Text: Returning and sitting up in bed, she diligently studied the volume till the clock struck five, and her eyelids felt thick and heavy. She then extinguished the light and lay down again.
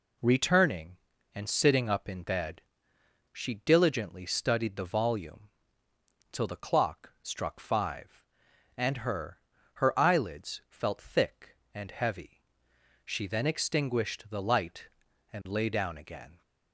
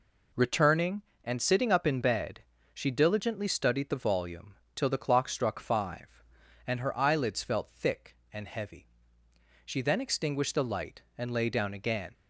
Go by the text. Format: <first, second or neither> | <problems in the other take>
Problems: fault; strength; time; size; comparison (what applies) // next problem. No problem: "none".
second | pauses between "volume" and "till"; noticeable; at 5.4 s; 0.84 s long; slight in the second // says "her" twice; at 9.7 s